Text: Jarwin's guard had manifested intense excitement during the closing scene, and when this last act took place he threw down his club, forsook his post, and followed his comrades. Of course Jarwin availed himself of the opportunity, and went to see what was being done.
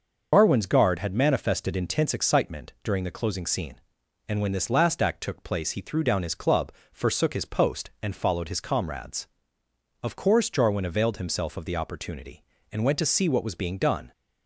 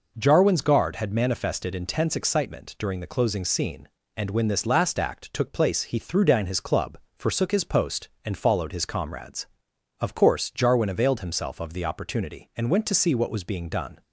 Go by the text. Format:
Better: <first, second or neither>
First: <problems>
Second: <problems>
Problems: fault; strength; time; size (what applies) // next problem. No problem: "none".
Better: second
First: loses the start of "Jarwin's"; at 0.3 s; 135 ms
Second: none